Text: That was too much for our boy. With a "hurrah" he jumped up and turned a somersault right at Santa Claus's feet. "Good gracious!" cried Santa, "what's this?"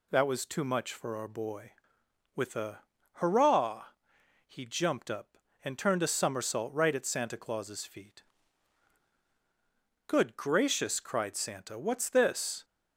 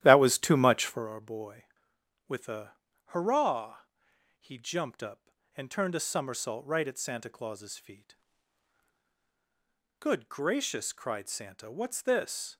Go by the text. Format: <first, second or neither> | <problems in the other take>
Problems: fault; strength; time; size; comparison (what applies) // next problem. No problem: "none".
first | starts louder than the rest; strong; until 1.1 s; 12.5 dB // pauses between "a" and "hurrah"; slight; at 2.7 s; 0.34 s long; slight in the first // pauses between "hurrah" and "he"; noticeable; at 3.8 s; 0.58 s long; noticeable in the first